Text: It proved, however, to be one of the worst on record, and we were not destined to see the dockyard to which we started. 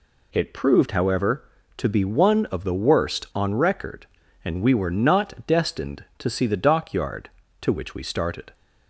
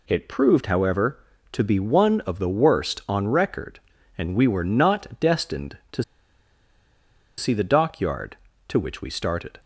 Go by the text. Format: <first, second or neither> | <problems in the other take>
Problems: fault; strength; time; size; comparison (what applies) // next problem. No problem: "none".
first | pauses between "to" and "see"; strong; at 6.0 s; 1.3 s long